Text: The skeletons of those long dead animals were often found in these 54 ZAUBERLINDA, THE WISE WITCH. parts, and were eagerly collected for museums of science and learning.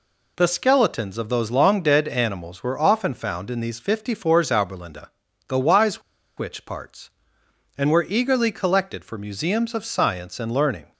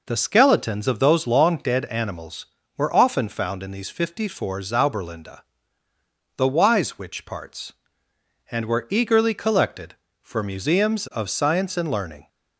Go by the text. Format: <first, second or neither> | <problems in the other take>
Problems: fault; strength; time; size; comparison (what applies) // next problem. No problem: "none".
second | pauses between "WISE" and "WITCH"; at 6.0 s; 0.36 s long